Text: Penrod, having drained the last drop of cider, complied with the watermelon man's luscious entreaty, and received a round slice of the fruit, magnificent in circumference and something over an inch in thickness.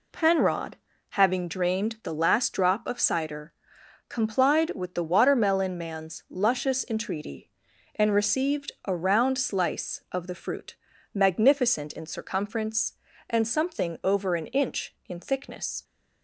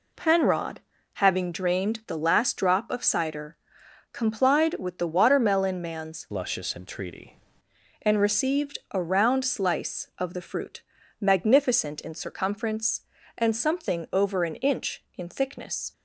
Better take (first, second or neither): first